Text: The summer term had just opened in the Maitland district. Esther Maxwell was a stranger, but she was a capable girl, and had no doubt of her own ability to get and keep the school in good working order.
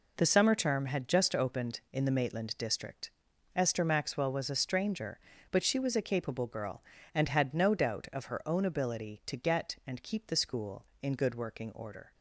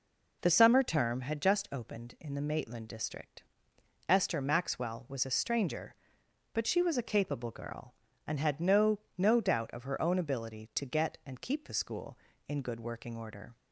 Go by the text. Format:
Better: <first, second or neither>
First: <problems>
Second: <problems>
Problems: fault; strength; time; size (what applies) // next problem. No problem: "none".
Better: first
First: none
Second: says "no" twice; at 9.1 s